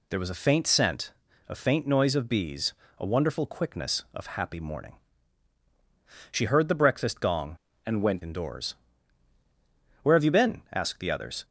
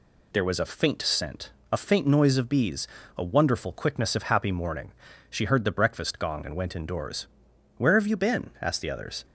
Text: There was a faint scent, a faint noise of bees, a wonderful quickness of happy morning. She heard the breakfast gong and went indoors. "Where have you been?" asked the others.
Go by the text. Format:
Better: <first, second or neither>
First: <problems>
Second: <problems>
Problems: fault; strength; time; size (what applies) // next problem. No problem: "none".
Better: second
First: changes voice from "and" to "went"; from 7.8 to 8.2 s; 0.4 s long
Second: none